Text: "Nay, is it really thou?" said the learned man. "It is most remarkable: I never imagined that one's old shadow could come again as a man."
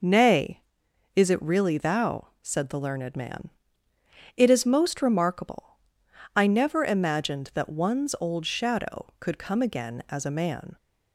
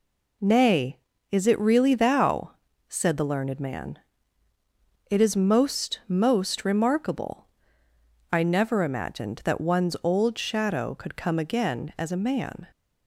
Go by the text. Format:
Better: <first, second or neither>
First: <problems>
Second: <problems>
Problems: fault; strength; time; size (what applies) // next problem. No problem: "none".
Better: first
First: none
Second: says "most" twice; at 6.0 s